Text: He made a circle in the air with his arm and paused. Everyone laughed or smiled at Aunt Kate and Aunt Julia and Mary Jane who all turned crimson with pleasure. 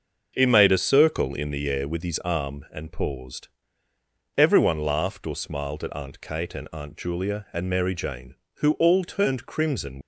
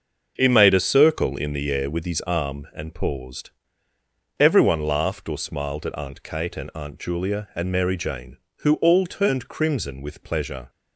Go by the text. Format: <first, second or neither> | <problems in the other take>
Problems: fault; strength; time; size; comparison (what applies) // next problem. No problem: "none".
second | starts louder than the rest; until 1.3 s; 6.5 dB; also in the second // stops before "with pleasure"; at 10.0 s